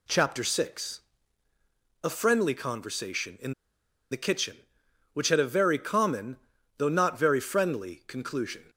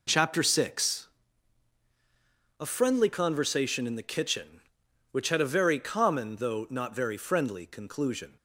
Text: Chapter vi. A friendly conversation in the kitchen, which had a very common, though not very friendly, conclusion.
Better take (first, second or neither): second